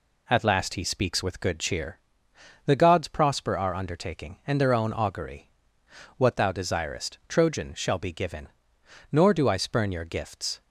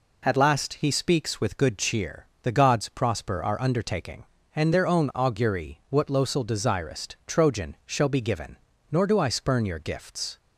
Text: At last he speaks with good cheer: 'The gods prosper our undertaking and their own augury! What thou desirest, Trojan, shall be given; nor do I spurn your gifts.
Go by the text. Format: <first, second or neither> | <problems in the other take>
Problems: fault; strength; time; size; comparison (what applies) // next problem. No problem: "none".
first | says "losel" for "thou"; at 6.0 s